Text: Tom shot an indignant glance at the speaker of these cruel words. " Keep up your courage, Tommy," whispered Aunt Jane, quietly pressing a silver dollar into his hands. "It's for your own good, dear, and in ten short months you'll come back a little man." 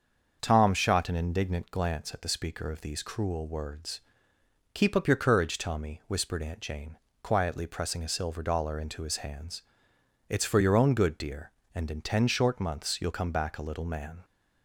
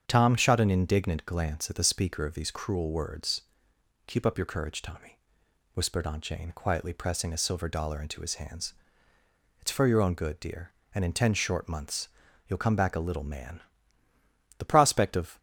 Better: first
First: starts louder than the rest; until 1.4 s; 7 dB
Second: starts louder than the rest; strong; until 1.0 s; 8 dB // pauses between "months" and "you'll"; at 12.0 s; 0.40 s long // goes on to say "The prospect of"; noticeable; from 14.5 s on; 0.80 s long

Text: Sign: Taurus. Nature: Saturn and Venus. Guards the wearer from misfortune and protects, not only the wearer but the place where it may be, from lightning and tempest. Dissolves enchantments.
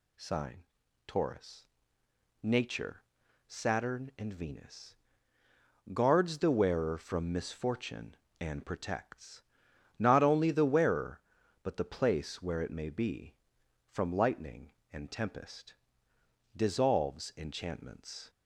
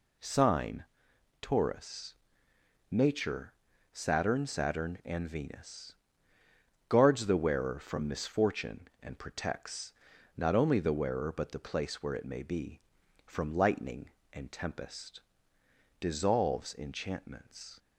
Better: first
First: none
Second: says "Saturn" twice; at 4.4 s

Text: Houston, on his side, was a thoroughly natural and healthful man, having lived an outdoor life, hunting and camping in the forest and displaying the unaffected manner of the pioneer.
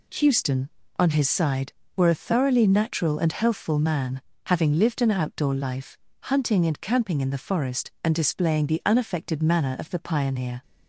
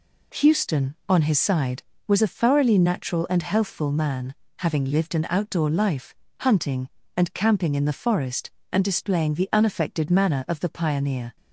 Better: second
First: says "were" for "was"; at 1.9 s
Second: none

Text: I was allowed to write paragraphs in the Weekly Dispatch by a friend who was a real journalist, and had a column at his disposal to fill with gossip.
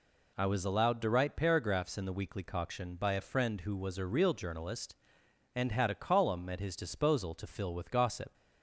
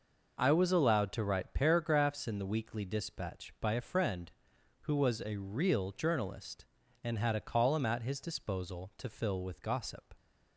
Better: second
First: says "Coction" for "Dispatch"; at 2.4 s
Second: none

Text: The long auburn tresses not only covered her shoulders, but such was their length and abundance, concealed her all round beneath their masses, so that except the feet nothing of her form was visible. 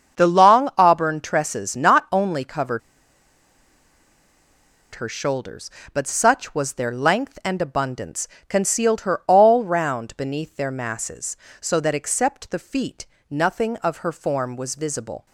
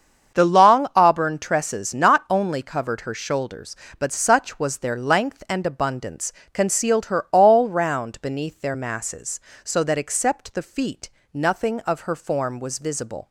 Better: second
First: starts louder than the rest; until 1.2 s; 7 dB // pauses between "covered" and "her"; strong; at 2.8 s; 2.1 s long // pauses between "feet" and "nothing"; slight; at 13.0 s; 0.24 s long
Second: starts louder than the rest; until 1.4 s; 7 dB // pauses between "feet" and "nothing"; slight; at 11.0 s; 0.24 s long

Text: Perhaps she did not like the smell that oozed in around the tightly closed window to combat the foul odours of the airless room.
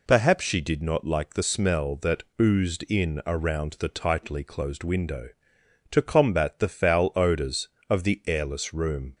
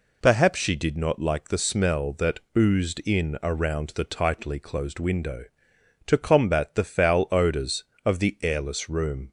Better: neither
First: pauses between "that" and "oozed"; slight; at 2.2 s; 0.16 s long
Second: pauses between "that" and "oozed"; slight; at 2.3 s; 0.16 s long

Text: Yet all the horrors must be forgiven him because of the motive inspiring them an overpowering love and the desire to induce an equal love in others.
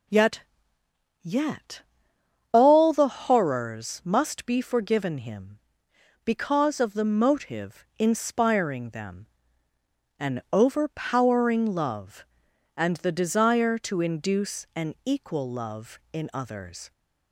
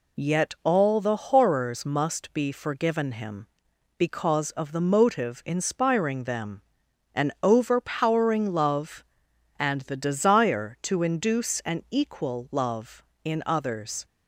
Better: second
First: says "Yet" twice; at 1.2 s // pauses between "them" and "an"; noticeable; at 9.2 s; 0.94 s long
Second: pauses between "them" and "an"; noticeable; at 6.6 s; 0.56 s long

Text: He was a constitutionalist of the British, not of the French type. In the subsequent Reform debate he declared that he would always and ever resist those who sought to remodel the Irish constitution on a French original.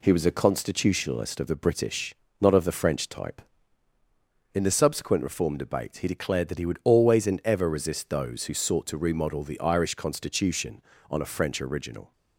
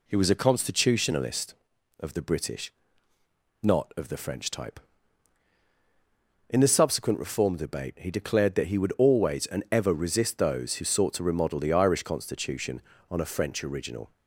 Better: neither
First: none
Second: none

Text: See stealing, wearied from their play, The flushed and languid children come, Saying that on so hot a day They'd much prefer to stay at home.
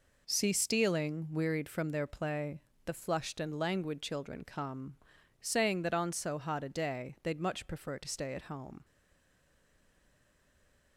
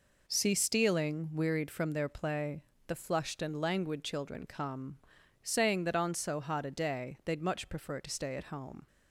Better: second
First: stays silent after the last word; from 8.8 s on; 2.1 s long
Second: none

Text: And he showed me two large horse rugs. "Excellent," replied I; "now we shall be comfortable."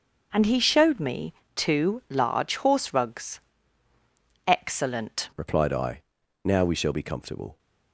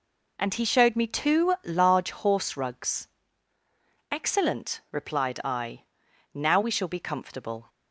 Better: second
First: pauses between "me" and "two"; slight; at 1.3 s; 0.24 s long // changes voice at "replied"; from 5.3 s on; 2.2 s long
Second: none

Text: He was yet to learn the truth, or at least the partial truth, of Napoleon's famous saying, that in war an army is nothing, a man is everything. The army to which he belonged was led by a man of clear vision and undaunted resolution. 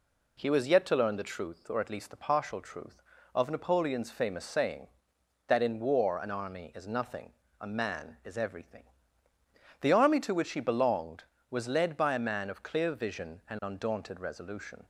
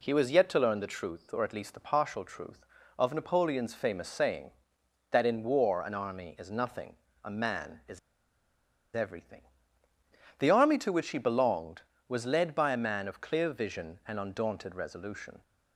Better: first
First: none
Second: pauses between "is" and "everything"; noticeable; at 7.9 s; 0.97 s long

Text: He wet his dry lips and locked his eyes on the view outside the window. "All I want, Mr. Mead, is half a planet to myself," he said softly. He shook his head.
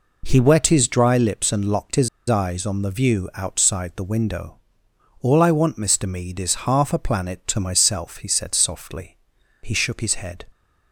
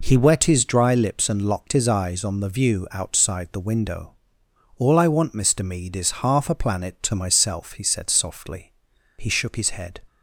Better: second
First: pauses between "his" and "eyes"; slight; at 2.0 s; 0.20 s long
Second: none

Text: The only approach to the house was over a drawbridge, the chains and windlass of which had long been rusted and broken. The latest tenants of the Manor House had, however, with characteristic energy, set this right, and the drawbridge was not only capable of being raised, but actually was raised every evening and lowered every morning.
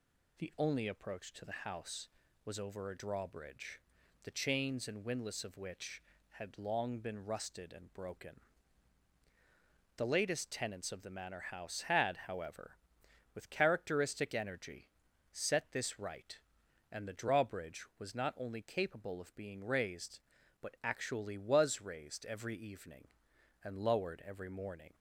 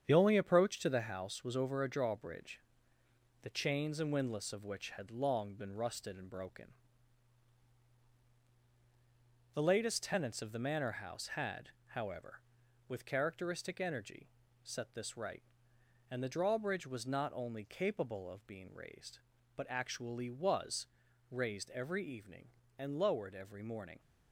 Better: first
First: none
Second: gets quieter; noticeable; throughout; 5.5 dB // pauses between "was" and "raised"; noticeable; at 20.8 s; 0.46 s long

